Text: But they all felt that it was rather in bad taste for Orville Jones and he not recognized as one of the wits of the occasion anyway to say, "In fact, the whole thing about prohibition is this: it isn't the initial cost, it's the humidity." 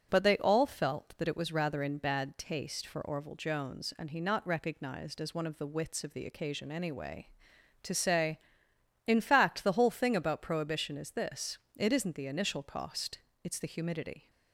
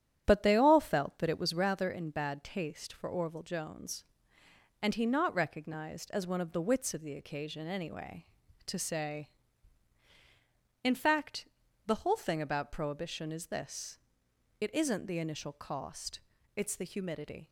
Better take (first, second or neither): first